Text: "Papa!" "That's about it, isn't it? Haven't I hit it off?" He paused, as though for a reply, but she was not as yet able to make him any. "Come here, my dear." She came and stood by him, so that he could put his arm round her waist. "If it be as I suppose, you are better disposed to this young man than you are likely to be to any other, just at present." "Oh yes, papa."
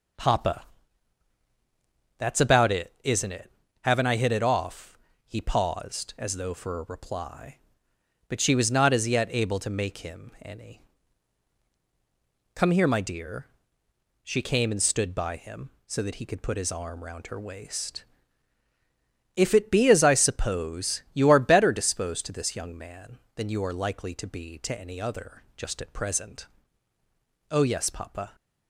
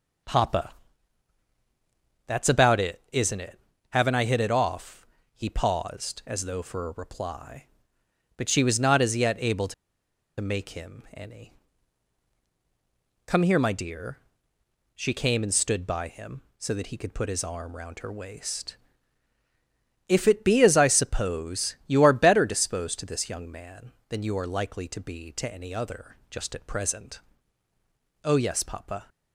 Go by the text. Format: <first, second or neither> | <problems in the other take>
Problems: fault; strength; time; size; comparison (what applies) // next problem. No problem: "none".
first | pauses between "to" and "make"; noticeable; at 9.7 s; 0.66 s long